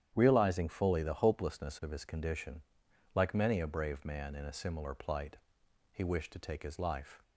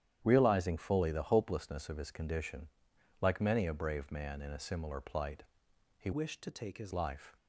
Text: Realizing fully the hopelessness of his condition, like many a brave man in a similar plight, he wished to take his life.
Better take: first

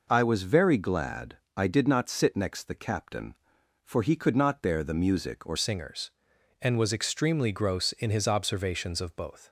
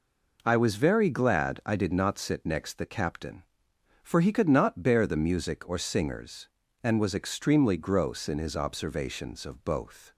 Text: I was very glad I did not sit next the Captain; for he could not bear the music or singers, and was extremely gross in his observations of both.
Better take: second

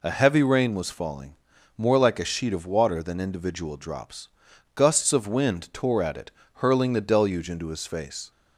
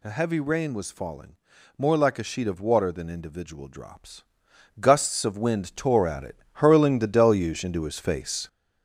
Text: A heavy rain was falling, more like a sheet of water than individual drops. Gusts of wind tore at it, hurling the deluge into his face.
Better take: first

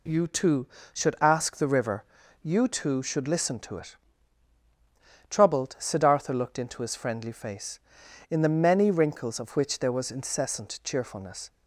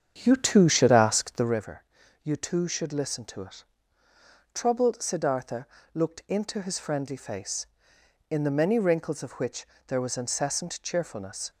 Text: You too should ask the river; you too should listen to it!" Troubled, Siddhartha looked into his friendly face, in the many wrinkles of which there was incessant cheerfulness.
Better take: first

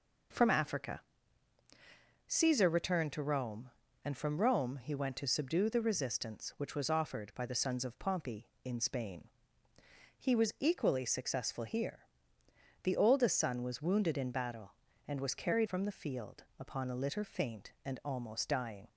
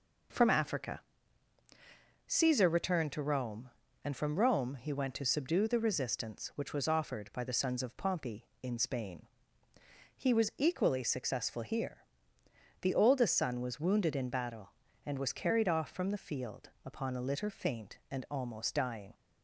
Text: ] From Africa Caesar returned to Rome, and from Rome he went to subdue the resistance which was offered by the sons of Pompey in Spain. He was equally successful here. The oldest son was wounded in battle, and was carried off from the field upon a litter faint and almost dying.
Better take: second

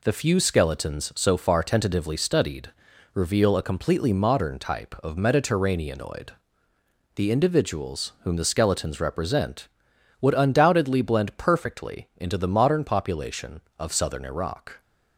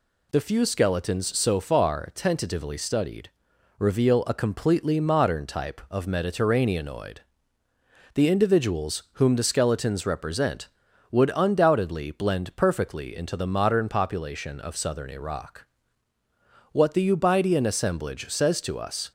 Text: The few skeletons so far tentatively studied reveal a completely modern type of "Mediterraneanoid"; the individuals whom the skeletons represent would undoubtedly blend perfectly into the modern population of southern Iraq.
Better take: first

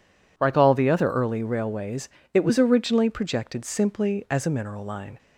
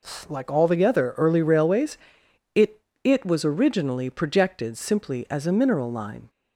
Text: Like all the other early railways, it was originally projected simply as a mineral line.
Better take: first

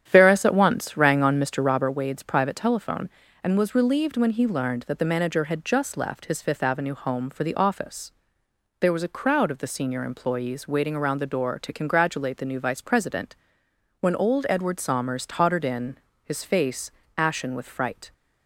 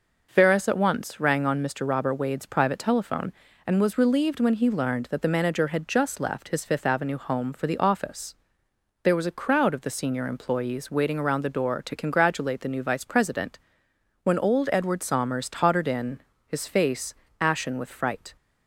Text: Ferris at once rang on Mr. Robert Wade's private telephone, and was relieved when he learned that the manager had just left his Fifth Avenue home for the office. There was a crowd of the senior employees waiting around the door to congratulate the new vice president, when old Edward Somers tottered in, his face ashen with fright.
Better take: second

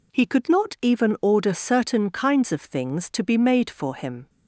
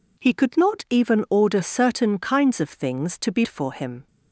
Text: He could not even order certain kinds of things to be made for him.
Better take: first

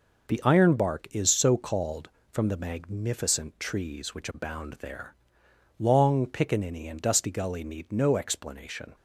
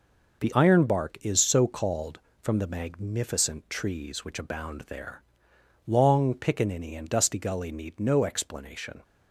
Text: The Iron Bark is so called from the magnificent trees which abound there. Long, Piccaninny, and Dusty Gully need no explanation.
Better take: neither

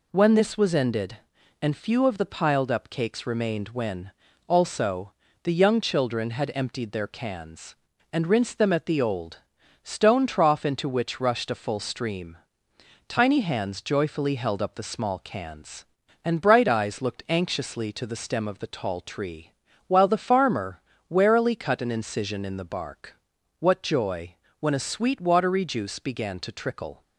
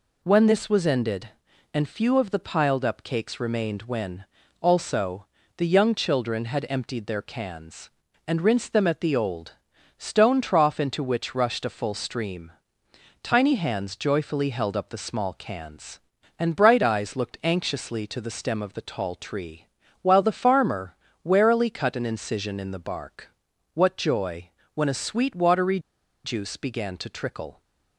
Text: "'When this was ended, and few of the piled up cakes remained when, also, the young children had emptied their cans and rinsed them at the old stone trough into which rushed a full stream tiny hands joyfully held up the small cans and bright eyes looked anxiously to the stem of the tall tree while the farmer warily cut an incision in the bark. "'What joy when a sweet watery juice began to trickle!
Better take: first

